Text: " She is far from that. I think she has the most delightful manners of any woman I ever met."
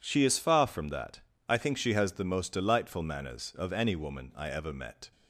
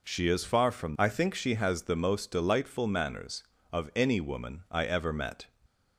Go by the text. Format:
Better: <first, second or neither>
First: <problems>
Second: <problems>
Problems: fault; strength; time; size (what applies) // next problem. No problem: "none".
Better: first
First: none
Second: skips "that"; at 0.9 s